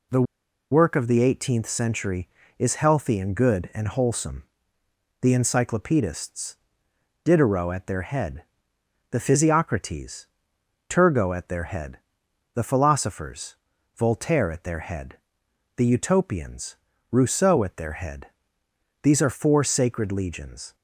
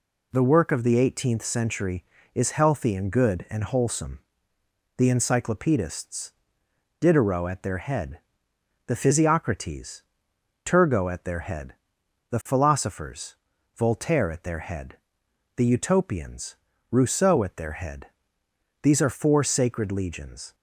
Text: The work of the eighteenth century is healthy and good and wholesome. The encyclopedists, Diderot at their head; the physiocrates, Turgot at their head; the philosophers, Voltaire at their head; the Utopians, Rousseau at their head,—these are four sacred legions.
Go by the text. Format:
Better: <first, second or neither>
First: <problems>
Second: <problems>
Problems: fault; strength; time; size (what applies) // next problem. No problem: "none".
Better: second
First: pauses between "The" and "work"; noticeable; at 0.2 s; 0.50 s long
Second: none